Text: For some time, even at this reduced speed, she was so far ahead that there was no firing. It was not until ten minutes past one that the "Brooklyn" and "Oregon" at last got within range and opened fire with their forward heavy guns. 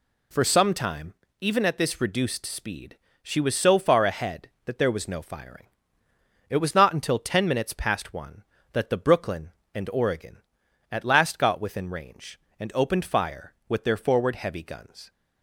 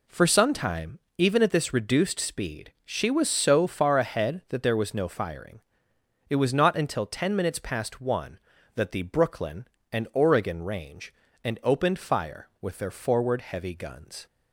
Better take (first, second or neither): first